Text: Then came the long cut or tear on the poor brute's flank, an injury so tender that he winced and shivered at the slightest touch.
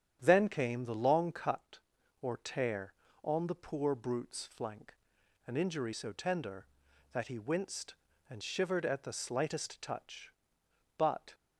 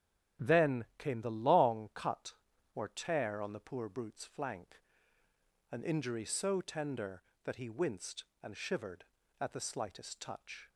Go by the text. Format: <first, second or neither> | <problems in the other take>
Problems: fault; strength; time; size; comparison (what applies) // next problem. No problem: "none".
second | starts louder than the rest; strong; until 1.2 s; 9.5 dB; strong in the second // goes on to say "But"; slight; from 10.9 s on; 0.36 s long